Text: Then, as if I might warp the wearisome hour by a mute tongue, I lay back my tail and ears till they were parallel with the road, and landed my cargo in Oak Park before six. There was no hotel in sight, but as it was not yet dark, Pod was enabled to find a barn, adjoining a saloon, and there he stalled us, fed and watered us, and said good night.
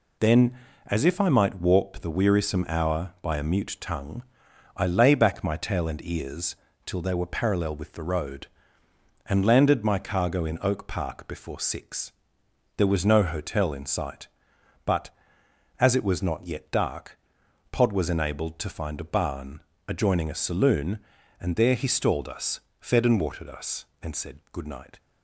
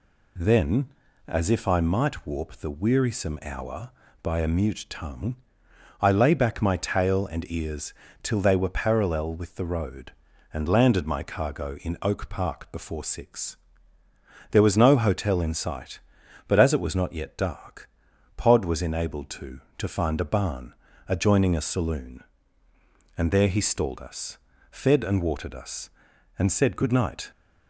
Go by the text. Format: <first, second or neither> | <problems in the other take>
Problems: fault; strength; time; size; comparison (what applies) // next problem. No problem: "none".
first | pauses between "ears" and "till"; slight; at 7.9 s; 0.28 s long; slight in the first // says "to" twice; at 19.7 s